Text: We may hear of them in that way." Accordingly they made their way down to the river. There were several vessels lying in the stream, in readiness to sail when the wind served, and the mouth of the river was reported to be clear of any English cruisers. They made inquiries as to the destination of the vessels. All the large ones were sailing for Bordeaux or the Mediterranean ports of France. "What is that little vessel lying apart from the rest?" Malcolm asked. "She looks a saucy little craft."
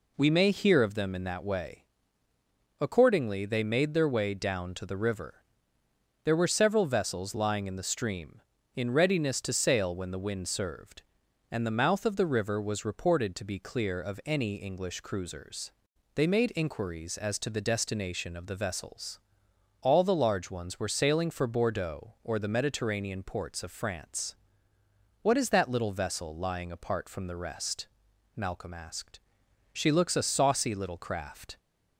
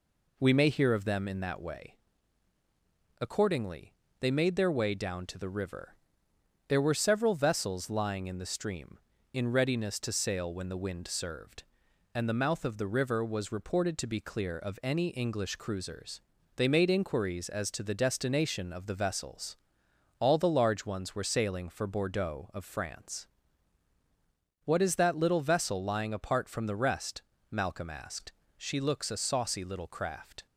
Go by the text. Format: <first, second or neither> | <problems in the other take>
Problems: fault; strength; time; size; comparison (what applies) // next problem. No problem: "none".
first | pauses between "Accordingly" and "they"; slight; at 3.9 s; 0.26 s long // skips "or the Mediterranean ports"; at 22.5 s